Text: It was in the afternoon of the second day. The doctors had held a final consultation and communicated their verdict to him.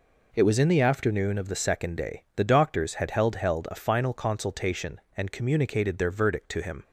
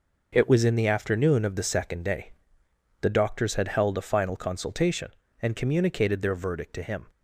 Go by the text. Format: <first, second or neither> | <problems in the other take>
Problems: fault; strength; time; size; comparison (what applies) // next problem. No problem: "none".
second | says "held" twice; at 3.3 s